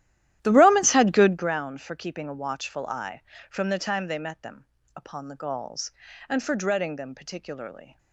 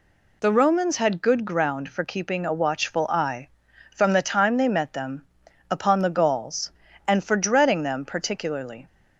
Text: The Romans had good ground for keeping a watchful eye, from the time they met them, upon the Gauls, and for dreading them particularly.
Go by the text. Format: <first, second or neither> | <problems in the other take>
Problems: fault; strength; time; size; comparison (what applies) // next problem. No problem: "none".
second | starts louder than the rest; strong; until 1.5 s; 13 dB